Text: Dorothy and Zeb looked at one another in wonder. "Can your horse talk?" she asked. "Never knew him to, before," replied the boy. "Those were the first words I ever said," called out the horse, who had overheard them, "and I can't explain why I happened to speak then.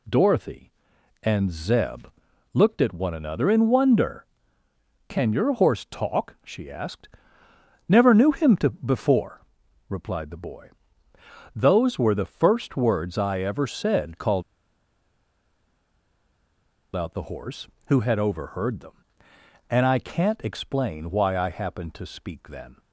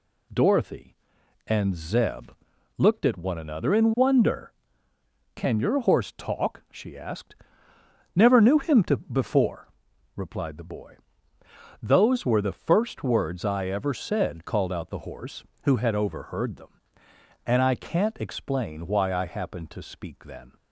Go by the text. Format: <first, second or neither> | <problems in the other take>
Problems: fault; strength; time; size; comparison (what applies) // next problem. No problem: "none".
second | pauses between "Zeb" and "looked"; noticeable; at 2.0 s; 0.46 s long; noticeable in the second // pauses between "called" and "out"; strong; at 14.4 s; 2.5 s long